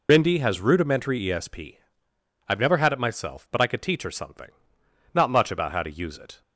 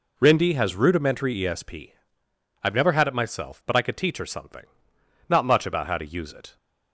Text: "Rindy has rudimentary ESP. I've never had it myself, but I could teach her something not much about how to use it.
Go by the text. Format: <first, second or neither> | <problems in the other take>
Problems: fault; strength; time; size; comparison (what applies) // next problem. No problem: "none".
second | loses the start of "Rindy"; at 0.0 s; 60 ms // pauses between "something" and "not"; noticeable; at 4.4 s; 0.64 s long; noticeable in the second